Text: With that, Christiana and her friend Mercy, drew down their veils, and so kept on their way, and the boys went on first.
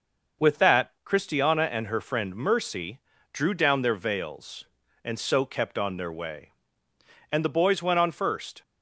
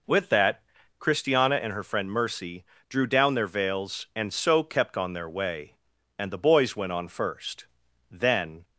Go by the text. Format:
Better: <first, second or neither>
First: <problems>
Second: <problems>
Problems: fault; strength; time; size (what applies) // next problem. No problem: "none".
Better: first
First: none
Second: goes on to say "Then"; from 8.0 s on; 0.54 s long